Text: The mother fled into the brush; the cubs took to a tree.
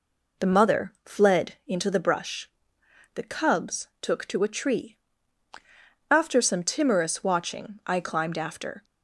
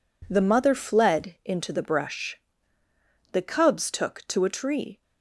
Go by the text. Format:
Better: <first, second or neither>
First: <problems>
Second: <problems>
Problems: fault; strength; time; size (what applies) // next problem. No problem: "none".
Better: second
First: goes on to say "After some timorous watching I climbed after"; strong; from 6.0 s on; 2.7 s long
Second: none